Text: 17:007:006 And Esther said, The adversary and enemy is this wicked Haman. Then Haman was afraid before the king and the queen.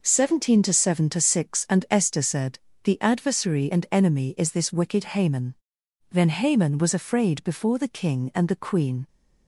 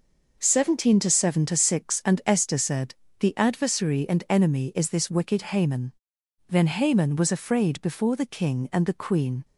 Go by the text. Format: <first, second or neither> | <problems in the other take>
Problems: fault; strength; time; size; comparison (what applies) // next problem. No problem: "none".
neither | none